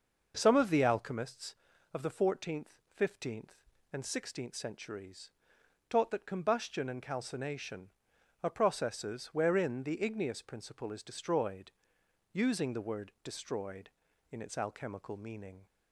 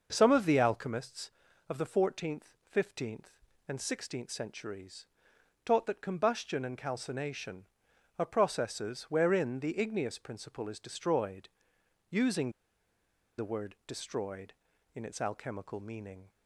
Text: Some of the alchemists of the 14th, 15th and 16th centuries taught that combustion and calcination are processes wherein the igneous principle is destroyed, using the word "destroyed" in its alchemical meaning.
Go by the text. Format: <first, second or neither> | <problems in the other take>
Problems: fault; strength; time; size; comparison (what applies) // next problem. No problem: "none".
first | starts louder than the rest; noticeable; until 1.1 s; 6 dB; noticeable in the first // pauses between "centuries" and "taught"; noticeable; at 5.0 s; 0.60 s long; noticeable in the first // pauses between "using" and "the"; noticeable; at 12.5 s; 0.87 s long